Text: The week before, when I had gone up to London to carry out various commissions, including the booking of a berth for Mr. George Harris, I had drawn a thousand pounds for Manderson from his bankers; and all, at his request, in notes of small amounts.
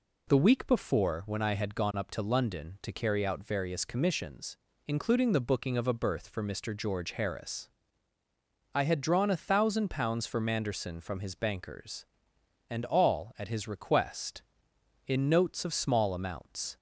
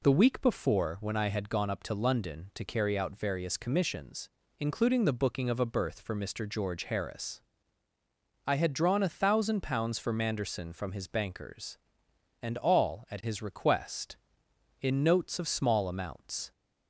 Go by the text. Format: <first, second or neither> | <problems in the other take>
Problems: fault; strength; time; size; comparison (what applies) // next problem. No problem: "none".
neither | none